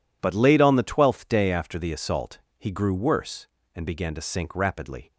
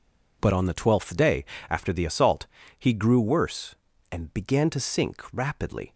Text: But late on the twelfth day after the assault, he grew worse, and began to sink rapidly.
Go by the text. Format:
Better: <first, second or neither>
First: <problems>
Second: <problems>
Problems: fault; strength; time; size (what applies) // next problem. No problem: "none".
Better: first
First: none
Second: skips "late"; at 0.5 s // pauses between "day" and "after"; slight; at 1.4 s; 0.24 s long